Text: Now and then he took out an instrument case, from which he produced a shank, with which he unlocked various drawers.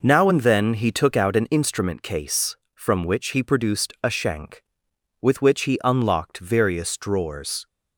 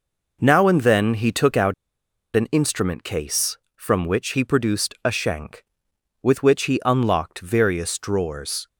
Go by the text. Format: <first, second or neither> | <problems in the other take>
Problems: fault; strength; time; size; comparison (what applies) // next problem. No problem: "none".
first | pauses between "out" and "an"; noticeable; at 1.7 s; 0.61 s long